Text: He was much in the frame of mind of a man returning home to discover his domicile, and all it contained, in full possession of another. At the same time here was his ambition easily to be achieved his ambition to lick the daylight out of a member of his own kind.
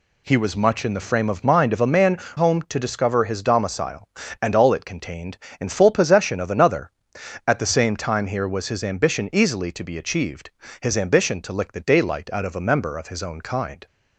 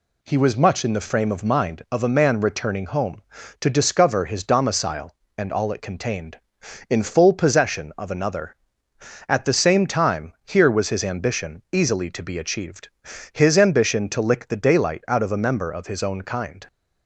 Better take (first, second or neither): second